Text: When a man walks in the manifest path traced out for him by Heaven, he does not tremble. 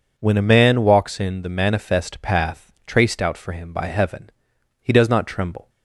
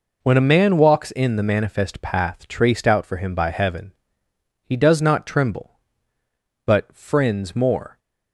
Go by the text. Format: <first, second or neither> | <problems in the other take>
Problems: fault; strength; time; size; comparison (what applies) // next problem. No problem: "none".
first | goes on to say "But friends more"; from 6.6 s on; 1.3 s long